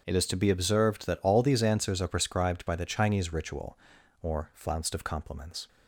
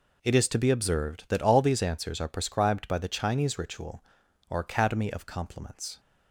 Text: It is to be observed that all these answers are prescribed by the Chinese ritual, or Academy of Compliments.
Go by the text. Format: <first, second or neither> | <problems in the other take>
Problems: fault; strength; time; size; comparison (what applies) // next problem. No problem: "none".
second | starts louder than the rest; strong; until 1.0 s; 7 dB // says "Flounced" for "Academy"; at 4.5 s